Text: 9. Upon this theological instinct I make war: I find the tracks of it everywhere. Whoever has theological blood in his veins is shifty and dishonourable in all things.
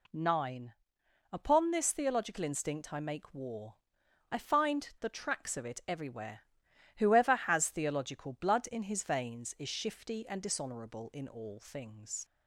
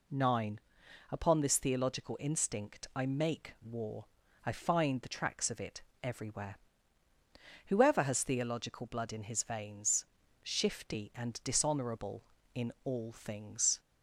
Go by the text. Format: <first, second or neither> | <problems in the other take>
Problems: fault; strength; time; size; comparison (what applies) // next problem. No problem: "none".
first | pauses between "it" and "everywhere"; slight; at 5.8 s; 0.20 s long // skips "is"; at 10.2 s